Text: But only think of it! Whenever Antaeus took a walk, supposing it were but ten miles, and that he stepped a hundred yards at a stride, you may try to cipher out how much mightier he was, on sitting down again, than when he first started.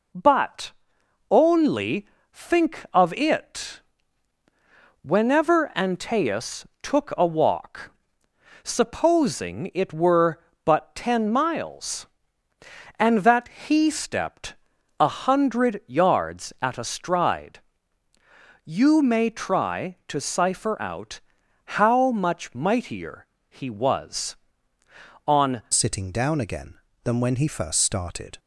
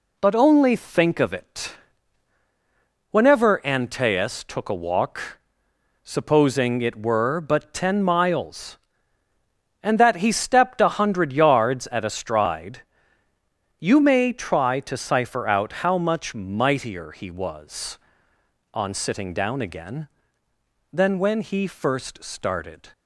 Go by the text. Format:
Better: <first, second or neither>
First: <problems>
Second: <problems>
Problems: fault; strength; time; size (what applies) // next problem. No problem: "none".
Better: second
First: pauses between "But" and "only"; noticeable; at 0.7 s; 0.58 s long // pauses between "only" and "think"; slight; at 2.0 s; 0.26 s long // pauses between "Antaeus" and "took"; slight; at 6.6 s; 0.16 s long // pauses between "that" and "he"; slight; at 13.4 s; 0.18 s long // pauses between "stepped" and "a"; noticeable; at 14.5 s; 0.46 s long // pauses between "out" and "how"; noticeable; at 21.1 s; 0.46 s long // pauses between "mightier" and "he"; slight; at 23.2 s; 0.22 s long // changes voice at "sitting"; from 25.7 s on; 2.6 s long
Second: none